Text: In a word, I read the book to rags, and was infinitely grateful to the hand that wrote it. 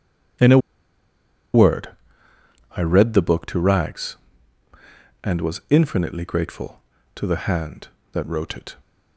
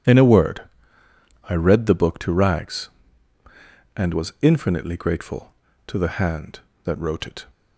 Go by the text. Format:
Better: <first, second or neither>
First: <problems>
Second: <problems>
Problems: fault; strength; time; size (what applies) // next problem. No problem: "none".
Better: second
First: pauses between "a" and "word"; noticeable; at 0.5 s; 0.95 s long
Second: none